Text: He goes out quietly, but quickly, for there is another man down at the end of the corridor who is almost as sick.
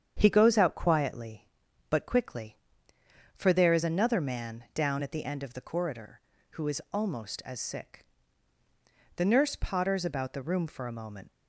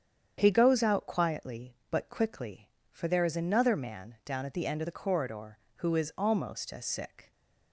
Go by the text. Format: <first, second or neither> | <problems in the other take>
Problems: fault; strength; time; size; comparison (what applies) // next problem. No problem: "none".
second | starts louder than the rest; strong; until 1.1 s; 8 dB; strong in the second // goes on to say "The nurse potters about the room for a moment"; strong; from 9.1 s on; 2.1 s long